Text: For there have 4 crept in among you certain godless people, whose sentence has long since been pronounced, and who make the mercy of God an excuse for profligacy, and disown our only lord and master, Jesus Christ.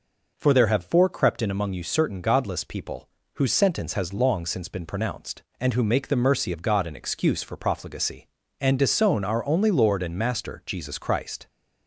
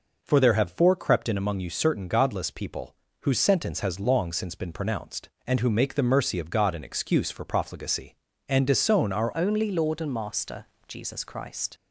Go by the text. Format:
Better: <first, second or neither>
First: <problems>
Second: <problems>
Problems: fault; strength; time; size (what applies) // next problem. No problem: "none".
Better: first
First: none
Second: changes voice at "only"; from 9.3 s on; 2.4 s long